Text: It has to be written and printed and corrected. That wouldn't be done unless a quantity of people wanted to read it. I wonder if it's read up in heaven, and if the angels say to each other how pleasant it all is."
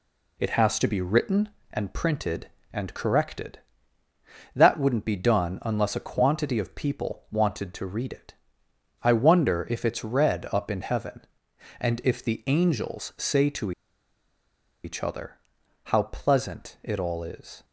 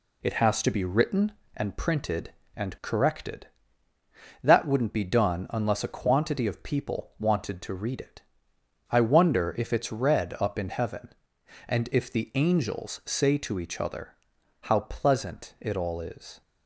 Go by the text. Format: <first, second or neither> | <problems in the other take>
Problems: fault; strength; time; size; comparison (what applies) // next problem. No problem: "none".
second | pauses between "to" and "each"; at 13.7 s; 1.1 s long // pauses between "other" and "how"; noticeable; at 15.3 s; 0.48 s long; noticeable in the second